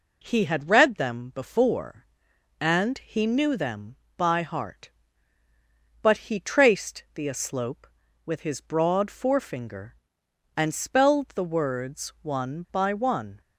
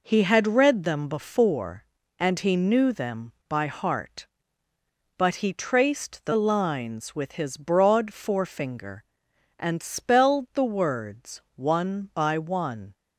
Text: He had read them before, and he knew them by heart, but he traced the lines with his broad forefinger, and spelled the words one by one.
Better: second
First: says "aslope" for "lines"; at 7.2 s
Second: none

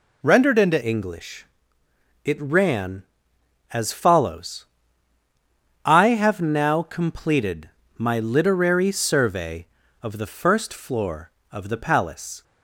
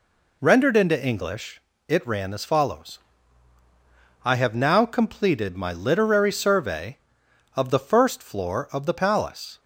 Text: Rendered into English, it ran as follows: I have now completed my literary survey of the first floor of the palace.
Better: second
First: changes voice at "English"; from 0.8 s on; 11.6 s long // pauses between "completed" and "my"; slight; at 7.7 s; 0.26 s long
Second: none

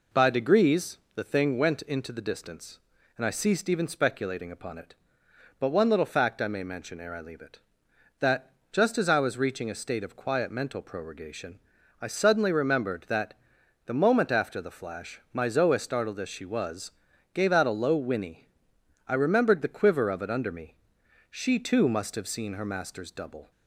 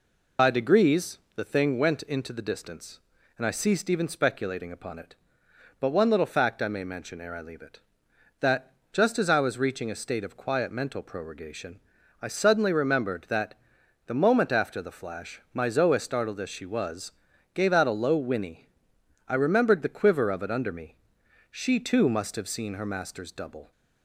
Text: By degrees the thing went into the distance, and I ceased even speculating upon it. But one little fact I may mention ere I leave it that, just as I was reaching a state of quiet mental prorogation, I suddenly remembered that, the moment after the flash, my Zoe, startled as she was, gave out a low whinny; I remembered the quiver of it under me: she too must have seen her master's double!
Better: first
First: pauses between "degrees" and "the"; slight; at 0.9 s; 0.16 s long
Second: loses the start of "By"; at 0.3 s; 65 ms // pauses between "degrees" and "the"; slight; at 1.1 s; 0.16 s long

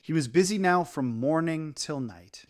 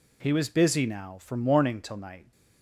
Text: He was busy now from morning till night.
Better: neither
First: none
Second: none

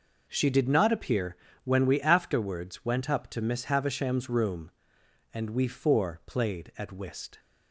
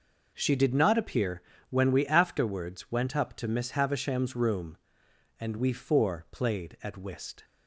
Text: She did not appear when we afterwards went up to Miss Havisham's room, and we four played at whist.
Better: neither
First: pauses between "appear" and "when"; slight; at 1.3 s; 0.26 s long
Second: pauses between "appear" and "when"; slight; at 1.4 s; 0.26 s long

